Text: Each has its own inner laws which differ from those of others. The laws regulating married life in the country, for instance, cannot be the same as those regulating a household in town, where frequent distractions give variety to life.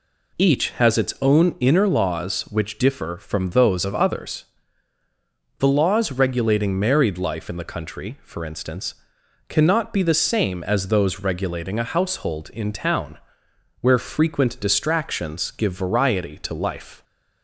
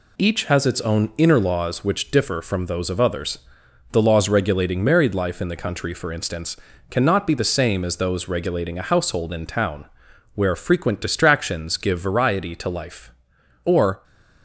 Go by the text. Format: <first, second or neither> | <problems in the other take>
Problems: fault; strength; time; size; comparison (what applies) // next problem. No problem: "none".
first | goes on to say "Or"; slight; from 13.6 s on; 0.40 s long